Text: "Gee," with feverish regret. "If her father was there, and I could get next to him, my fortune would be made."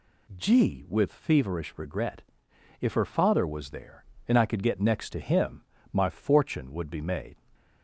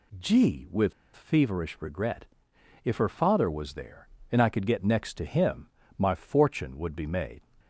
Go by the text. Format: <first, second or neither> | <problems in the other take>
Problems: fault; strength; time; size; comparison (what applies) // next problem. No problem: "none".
first | pauses between "with" and "feverish"; slight; at 0.9 s; 0.22 s long